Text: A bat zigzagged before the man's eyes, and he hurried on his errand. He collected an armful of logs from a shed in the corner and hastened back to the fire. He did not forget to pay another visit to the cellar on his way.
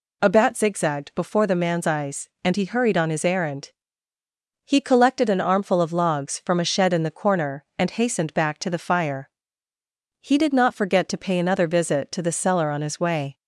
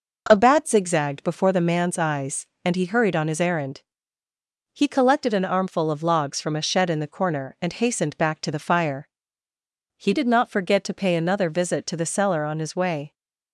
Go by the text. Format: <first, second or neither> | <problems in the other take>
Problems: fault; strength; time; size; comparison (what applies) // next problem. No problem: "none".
neither | none